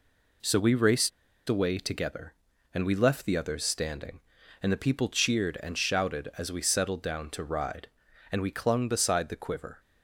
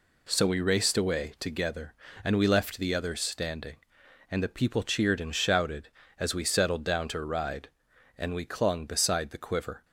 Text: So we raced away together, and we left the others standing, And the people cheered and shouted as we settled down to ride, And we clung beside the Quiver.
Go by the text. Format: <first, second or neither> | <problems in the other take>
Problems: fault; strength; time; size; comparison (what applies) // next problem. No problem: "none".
second | pauses between "raced" and "away"; at 1.1 s; 0.39 s long